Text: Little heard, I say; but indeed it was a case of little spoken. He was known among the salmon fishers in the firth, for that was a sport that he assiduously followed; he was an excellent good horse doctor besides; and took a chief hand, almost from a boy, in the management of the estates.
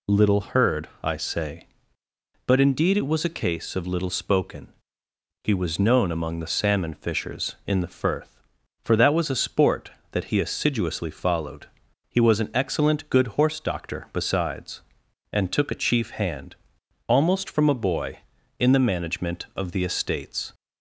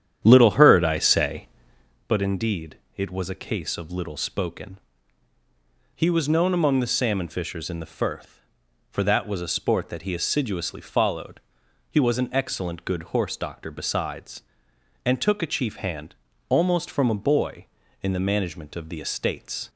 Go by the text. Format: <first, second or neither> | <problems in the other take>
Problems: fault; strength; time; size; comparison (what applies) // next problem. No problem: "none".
first | starts louder than the rest; strong; until 2.1 s; 9.5 dB // pauses between "indeed" and "it"; slight; at 2.7 s; 0.22 s long